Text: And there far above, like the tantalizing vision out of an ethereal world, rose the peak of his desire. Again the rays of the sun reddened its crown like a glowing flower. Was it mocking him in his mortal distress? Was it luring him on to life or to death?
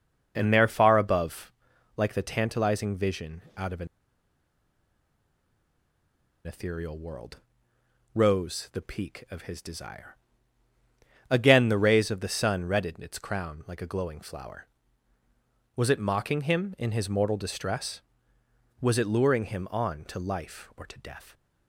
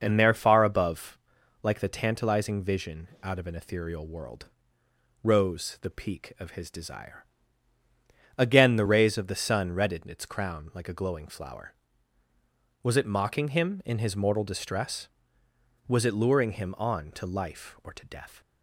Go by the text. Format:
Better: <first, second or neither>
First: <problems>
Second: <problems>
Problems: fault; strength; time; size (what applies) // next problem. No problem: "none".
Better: second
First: pauses between "vision" and "out"; slight; at 3.4 s; 0.16 s long // pauses between "an" and "ethereal"; strong; at 3.8 s; 2.5 s long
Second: pauses between "vision" and "out"; slight; at 3.0 s; 0.16 s long